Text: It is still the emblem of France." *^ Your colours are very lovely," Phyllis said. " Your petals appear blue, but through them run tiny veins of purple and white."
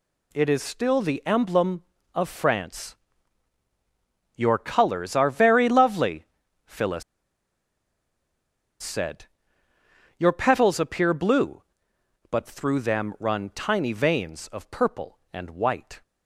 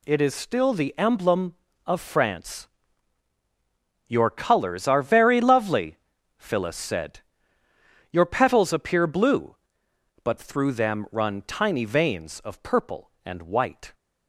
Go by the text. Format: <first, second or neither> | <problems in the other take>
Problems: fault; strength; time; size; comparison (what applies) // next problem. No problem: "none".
second | pauses between "Phyllis" and "said"; strong; at 7.0 s; 1.7 s long